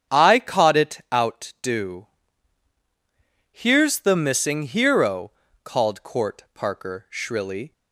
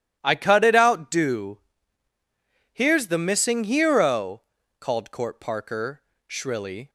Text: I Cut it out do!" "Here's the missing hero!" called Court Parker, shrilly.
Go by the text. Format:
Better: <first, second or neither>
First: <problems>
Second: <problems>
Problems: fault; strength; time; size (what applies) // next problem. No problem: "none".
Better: second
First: starts louder than the rest; strong; until 1.1 s; 8.5 dB // says "Caught" for "Cut"; at 0.3 s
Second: none